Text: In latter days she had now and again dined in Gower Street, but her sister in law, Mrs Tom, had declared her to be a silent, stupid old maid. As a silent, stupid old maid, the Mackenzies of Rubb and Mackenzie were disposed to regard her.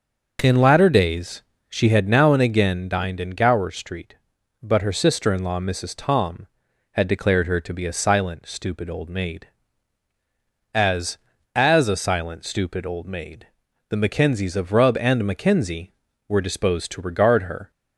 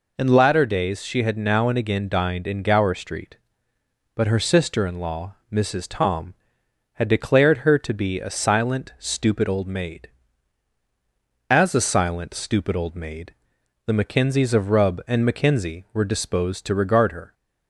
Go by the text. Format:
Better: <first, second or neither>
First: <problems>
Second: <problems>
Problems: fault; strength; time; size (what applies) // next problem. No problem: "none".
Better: second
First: pauses between "days" and "she"; slight; at 1.4 s; 0.26 s long // says "As" twice; at 11.5 s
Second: none